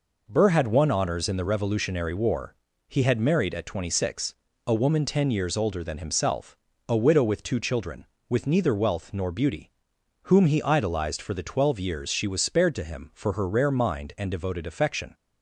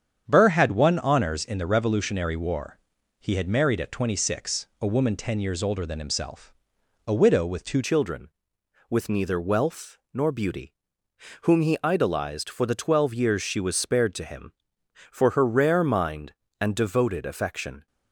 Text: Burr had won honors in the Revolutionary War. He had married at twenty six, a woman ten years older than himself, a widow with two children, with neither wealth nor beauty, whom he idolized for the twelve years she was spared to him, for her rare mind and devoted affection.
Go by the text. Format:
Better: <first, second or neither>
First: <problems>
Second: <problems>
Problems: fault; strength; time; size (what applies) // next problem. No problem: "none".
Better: first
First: none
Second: starts louder than the rest; strong; until 1.2 s; 8 dB // changes voice at "children"; from 7.8 s on; 10.0 s long // pauses between "wealth" and "nor"; slight; at 9.9 s; 0.16 s long